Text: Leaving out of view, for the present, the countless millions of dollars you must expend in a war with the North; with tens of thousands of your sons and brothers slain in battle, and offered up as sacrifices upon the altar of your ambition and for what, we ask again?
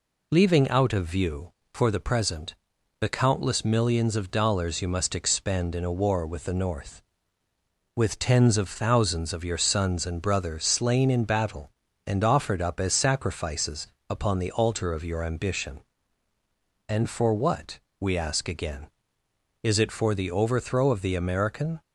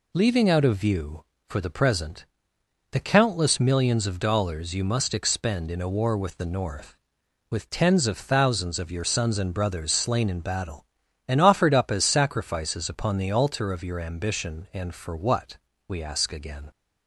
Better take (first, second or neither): second